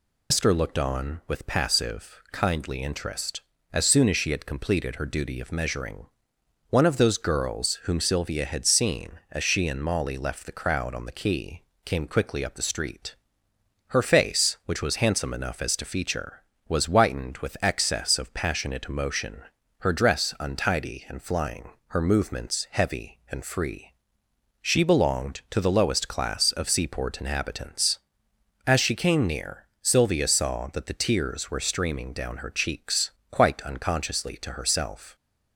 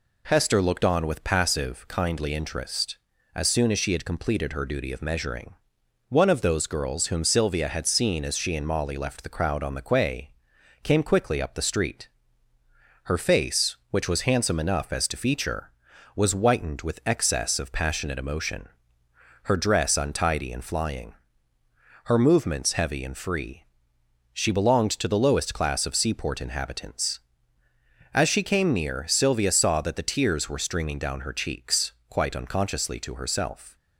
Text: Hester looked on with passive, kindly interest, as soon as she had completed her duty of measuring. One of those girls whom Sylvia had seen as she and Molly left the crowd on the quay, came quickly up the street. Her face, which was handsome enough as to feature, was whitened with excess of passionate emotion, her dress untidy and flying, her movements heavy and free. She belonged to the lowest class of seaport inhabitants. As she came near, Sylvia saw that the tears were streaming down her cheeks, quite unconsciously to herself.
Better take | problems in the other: second | loses the start of "Hester"; at 0.3 s; 110 ms

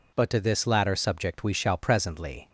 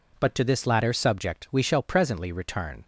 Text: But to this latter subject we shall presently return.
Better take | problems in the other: second | stops before "return"; at 2.4 s

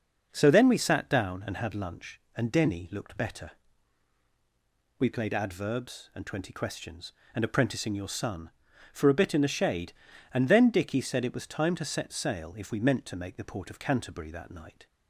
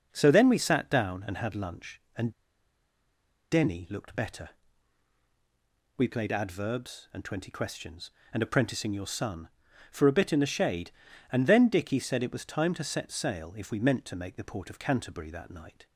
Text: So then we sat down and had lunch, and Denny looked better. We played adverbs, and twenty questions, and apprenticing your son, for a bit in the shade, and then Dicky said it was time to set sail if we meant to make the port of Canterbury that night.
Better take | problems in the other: first | pauses between "and" and "Denny"; at 2.3 s; 1.1 s long

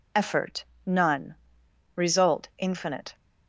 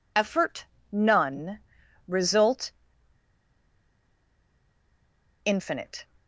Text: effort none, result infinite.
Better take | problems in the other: first | pauses between "effort" and "none"; slight; at 0.6 s; 0.24 s long; slight in the first // pauses between "result" and "infinite"; strong; at 2.7 s; 2.7 s long

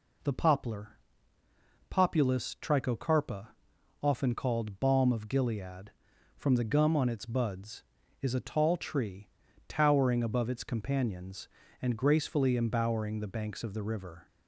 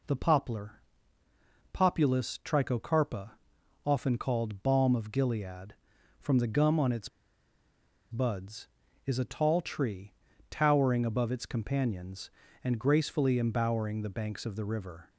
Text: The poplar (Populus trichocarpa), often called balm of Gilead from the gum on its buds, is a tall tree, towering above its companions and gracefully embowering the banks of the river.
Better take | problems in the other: first | pauses between "its" and "buds"; at 7.0 s; 1.0 s long

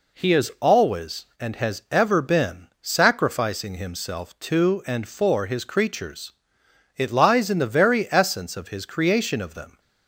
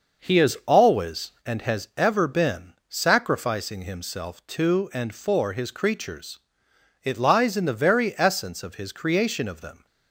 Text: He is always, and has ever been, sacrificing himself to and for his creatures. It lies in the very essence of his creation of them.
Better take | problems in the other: first | starts louder than the rest; noticeable; until 1.9 s; 5.5 dB

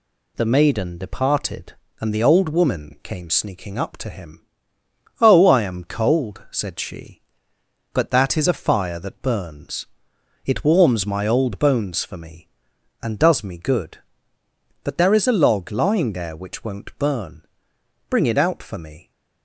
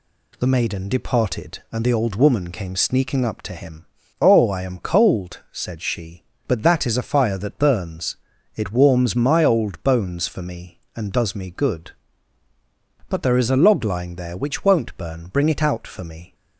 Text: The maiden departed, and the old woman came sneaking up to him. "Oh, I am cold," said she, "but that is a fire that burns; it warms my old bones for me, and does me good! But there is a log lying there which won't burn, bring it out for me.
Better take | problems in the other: neither | none

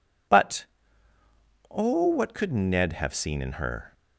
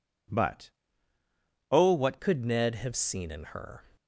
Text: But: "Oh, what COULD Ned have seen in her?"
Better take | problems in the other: first | changes voice at "COULD"; from 2.2 s on; 1.6 s long

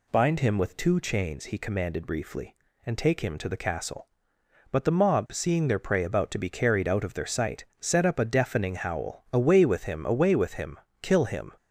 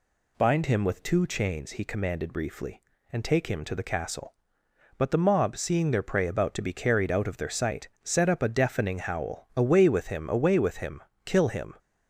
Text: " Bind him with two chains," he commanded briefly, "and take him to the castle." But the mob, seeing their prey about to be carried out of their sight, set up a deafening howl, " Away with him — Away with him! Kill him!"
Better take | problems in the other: neither | none

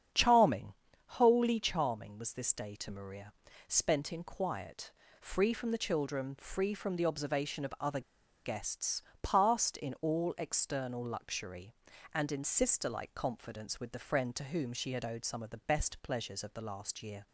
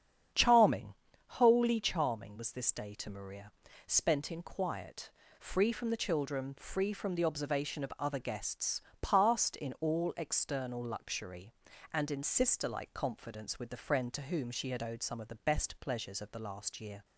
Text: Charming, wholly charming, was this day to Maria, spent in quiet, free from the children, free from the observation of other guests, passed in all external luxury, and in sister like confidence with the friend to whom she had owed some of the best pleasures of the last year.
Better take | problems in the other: second | starts louder than the rest; strong; until 1.4 s; 8 dB; strong in the second // pauses between "other" and "guests"; at 8.0 s; 0.42 s long

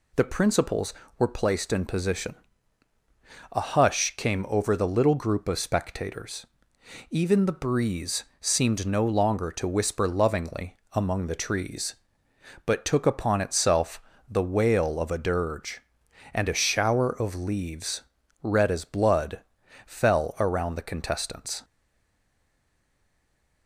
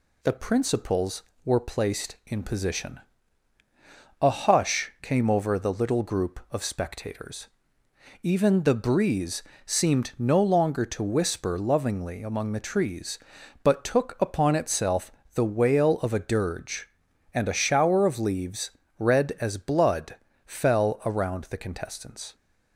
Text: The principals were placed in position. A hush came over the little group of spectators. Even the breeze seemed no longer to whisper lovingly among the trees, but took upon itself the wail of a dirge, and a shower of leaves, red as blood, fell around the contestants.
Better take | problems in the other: second | pauses between "breeze" and "seemed"; slight; at 8.2 s; 0.16 s long; slight in the second // pauses between "lovingly" and "among"; slight; at 10.7 s; 0.16 s long // pauses between "itself" and "the"; slight; at 14.0 s; 0.30 s long; slight in the second // stays silent after the last word; noticeable; from 21.6 s on; 2.0 s long

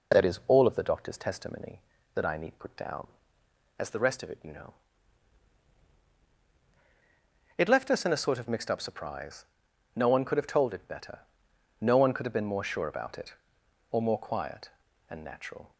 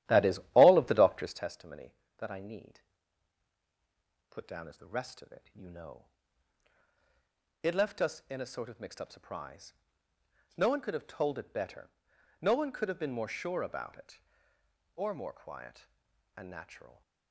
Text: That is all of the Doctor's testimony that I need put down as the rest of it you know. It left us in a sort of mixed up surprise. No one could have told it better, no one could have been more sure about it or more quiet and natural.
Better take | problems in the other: first | starts louder than the rest; strong; until 1.5 s; 12.5 dB // pauses between "need" and "put"; strong; at 2.7 s; 1.5 s long

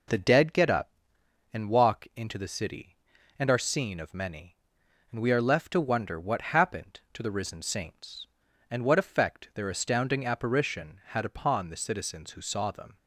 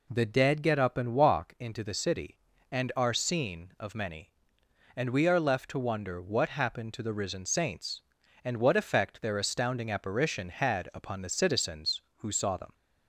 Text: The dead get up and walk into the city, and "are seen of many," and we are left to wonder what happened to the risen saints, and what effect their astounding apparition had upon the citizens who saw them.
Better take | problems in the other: neither | none

